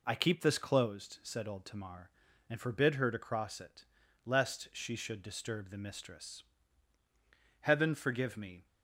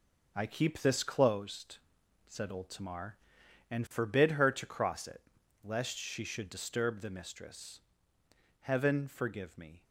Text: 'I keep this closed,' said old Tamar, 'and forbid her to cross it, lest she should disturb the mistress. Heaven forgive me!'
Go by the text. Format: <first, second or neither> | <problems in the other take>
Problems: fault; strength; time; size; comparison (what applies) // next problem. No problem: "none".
first | gets quieter; strong; throughout; 7.5 dB